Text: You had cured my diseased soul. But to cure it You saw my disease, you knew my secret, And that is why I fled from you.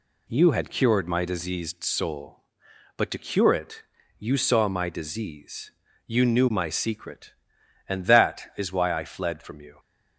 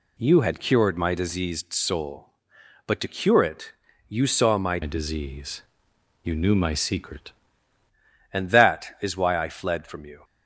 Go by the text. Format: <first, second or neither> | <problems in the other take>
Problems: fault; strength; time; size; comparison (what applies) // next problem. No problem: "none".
first | pauses between "it" and "You"; at 3.7 s; 0.38 s long; also in the first // changes voice from "disease" to "secret"; from 4.8 to 7.3 s; 2.5 s long